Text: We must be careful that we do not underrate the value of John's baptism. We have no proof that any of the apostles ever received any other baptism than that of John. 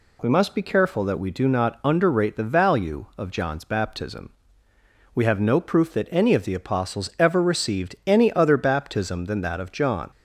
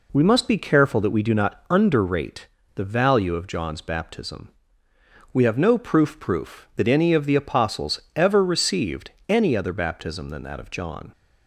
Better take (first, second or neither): first